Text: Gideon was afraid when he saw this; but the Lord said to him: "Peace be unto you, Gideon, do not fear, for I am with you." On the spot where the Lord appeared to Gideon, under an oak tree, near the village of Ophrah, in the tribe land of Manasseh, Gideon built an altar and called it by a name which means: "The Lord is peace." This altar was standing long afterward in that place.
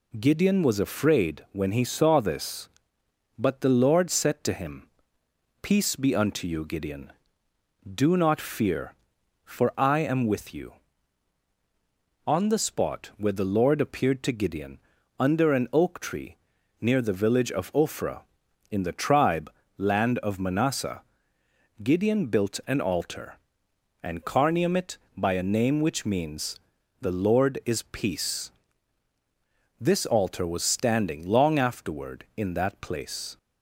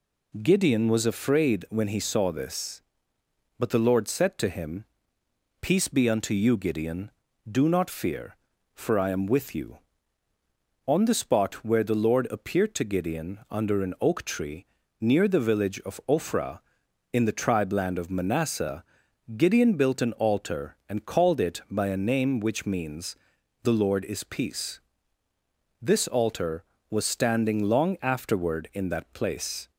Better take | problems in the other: second | pauses between "tribe" and "land"; slight; at 19.5 s; 0.26 s long // says "carnium" for "called"; at 24.2 s

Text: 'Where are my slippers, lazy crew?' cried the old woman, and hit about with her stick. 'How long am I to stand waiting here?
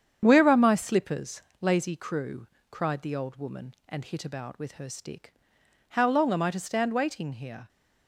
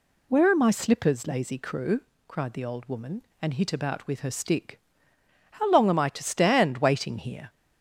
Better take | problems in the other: second | gets quieter; throughout; 6.5 dB

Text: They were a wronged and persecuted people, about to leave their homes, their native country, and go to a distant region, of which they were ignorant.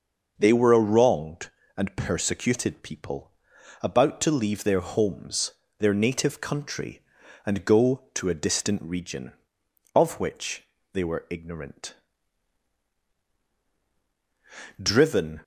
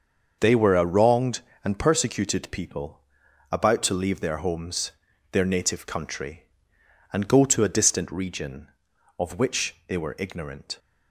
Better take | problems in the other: second | starts louder than the rest; noticeable; until 1.3 s; 6 dB; also in the second // pauses between "which" and "they"; slight; at 10.6 s; 0.30 s long // goes on to say "Driven"; from 14.8 s on; 0.60 s long

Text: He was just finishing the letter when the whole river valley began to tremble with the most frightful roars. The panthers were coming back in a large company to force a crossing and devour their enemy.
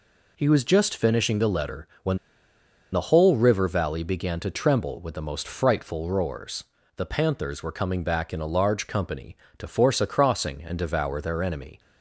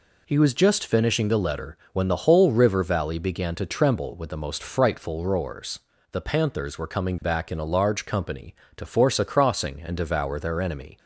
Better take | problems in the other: second | pauses between "letter" and "when"; slight; at 1.8 s; 0.16 s long; slight in the second // pauses between "when" and "the"; noticeable; at 2.1 s; 0.75 s long

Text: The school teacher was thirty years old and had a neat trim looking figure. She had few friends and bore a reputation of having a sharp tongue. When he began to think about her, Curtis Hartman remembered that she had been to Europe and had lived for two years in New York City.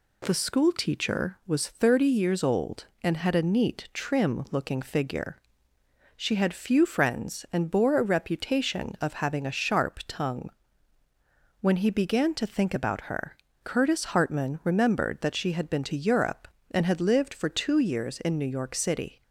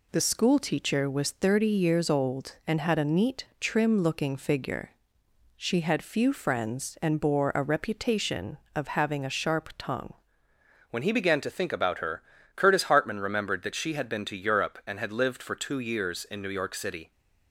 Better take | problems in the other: first | changes voice at "When"; from 10.8 s on; 6.3 s long

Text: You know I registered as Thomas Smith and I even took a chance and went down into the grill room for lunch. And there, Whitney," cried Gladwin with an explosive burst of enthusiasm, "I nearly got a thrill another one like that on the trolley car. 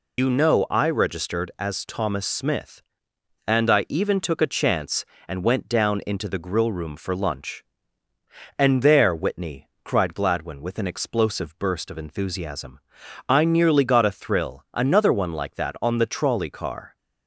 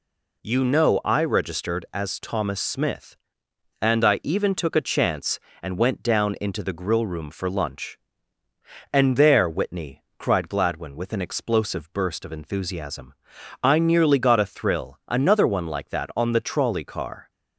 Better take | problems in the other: second | loses the start of "You"; at 0.1 s; 105 ms

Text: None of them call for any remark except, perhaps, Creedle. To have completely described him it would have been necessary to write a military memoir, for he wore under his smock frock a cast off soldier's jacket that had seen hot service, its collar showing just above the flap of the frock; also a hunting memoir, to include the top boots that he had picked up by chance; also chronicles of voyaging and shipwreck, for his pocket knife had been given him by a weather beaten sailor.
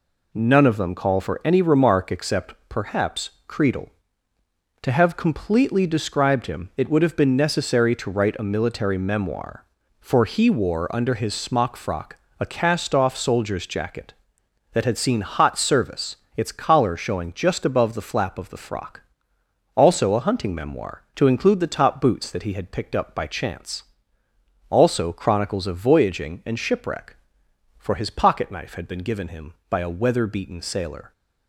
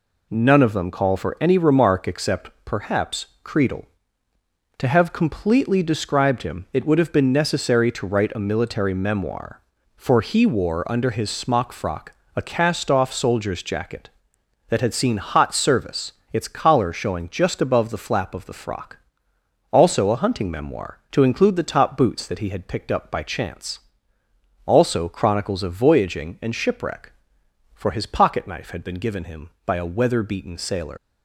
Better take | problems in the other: first | pauses between "frock" and "a"; slight; at 12.1 s; 0.22 s long; slight in the first // leaves "sailor" unfinished; at 30.9 s; 105 ms

